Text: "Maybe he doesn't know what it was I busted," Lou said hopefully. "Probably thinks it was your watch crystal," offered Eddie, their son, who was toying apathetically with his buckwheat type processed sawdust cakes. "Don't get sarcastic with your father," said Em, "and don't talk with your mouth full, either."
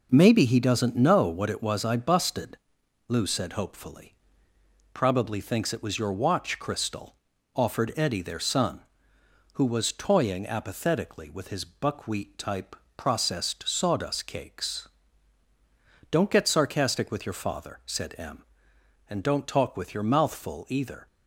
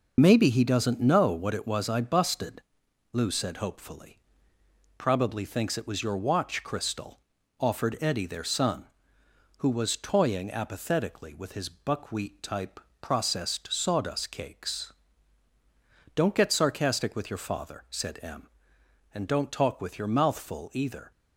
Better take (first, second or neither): first